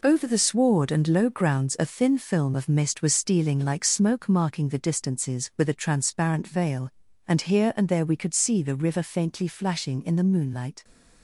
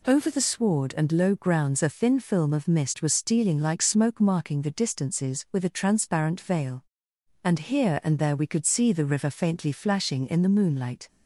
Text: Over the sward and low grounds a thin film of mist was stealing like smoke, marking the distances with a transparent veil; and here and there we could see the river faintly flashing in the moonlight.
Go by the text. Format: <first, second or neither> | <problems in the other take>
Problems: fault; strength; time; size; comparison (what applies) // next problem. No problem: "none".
second | gets quieter; strong; throughout; 7 dB